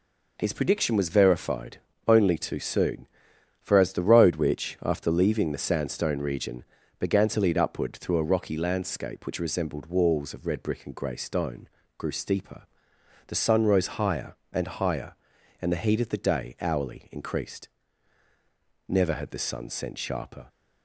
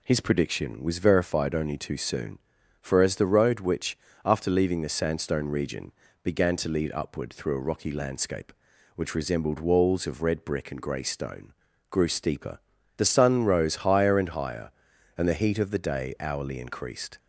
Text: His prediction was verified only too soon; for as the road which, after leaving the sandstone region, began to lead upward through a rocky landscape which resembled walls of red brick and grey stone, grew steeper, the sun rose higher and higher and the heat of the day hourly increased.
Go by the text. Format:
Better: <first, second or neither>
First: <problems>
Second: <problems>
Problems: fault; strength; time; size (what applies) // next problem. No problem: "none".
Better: second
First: pauses between "verified" and "only"; slight; at 1.7 s; 0.28 s long // goes on to say "Never had the sun sent sharper"; from 18.8 s on; 1.6 s long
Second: none